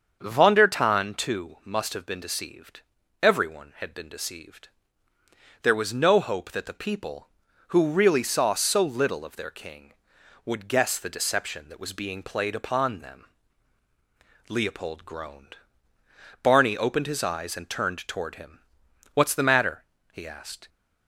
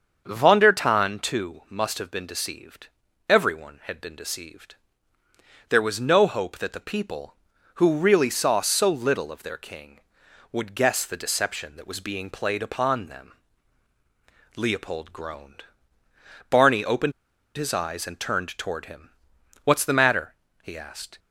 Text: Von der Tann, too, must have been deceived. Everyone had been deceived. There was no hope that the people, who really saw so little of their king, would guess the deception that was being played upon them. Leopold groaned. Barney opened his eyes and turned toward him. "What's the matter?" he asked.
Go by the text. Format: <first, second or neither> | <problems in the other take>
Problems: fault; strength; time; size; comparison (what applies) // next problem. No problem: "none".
first | starts louder than the rest; until 1.2 s; 7 dB; also in the first // pauses between "opened" and "his"; at 17.1 s; 0.44 s long